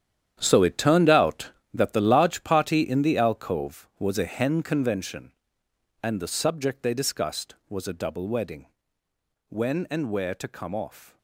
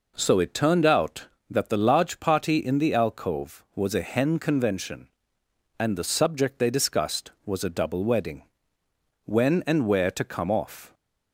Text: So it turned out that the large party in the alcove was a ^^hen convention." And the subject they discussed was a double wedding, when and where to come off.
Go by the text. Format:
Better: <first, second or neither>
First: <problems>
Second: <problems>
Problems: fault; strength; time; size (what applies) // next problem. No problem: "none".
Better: second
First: gets quieter; strong; throughout; 13 dB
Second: none